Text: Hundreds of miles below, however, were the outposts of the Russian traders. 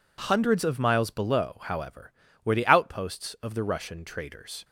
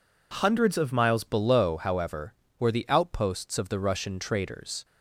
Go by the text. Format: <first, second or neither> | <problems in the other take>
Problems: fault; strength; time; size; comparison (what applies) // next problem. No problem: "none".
first | changes voice at "below"; from 1.2 s on; 3.6 s long